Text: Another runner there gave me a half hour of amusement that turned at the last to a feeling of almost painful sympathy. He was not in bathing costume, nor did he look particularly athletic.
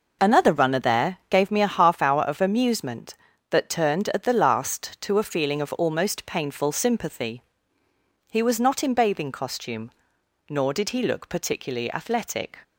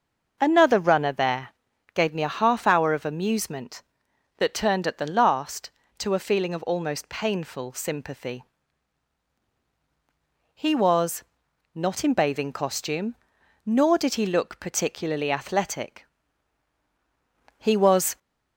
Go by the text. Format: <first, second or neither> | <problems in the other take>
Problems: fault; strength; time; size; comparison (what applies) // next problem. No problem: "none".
first | pauses between "there" and "gave"; at 1.4 s; 0.44 s long // pauses between "was" and "not"; noticeable; at 11.2 s; 0.50 s long // goes on to say "He was"; from 17.5 s on; 0.60 s long